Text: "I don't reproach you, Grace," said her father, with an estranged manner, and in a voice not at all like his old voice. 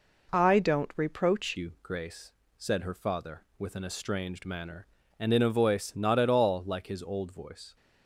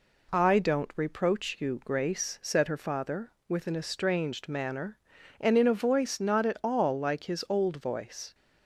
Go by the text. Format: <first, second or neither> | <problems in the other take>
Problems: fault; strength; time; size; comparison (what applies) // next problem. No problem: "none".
second | changes voice at "you"; from 1.5 s on; 6.2 s long